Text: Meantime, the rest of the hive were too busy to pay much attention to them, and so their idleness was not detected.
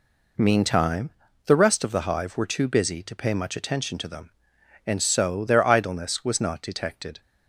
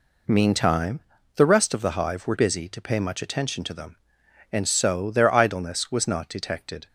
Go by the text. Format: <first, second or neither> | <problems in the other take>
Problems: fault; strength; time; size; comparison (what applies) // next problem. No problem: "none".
first | skips "too"; at 2.3 s